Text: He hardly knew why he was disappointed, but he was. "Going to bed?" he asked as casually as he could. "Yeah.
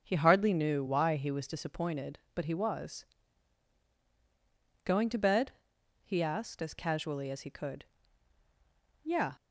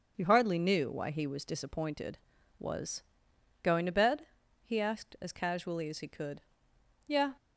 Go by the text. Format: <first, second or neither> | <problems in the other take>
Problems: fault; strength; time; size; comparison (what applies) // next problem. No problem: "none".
first | starts louder than the rest; until 1.1 s; 6.5 dB; also in the first // skips "but he"; at 2.3 s